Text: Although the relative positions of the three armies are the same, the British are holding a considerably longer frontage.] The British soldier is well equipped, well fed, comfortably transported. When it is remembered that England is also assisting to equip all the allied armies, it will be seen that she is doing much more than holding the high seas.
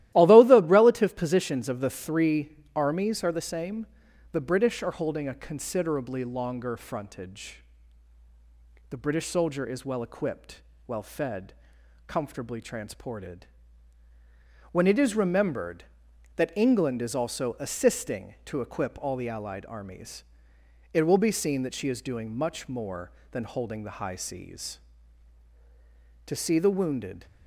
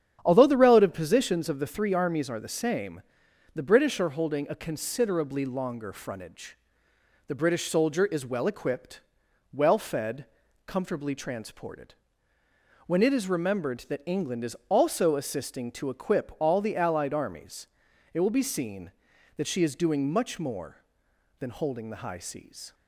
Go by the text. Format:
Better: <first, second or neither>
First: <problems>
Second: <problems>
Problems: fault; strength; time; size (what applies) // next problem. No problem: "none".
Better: second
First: starts louder than the rest; strong; until 1.1 s; 14.5 dB // pauses between "three" and "armies"; slight; at 2.5 s; 0.20 s long // goes on to say "To see the wounded"; noticeable; from 26.2 s on; 1.0 s long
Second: starts louder than the rest; strong; until 1.2 s; 9 dB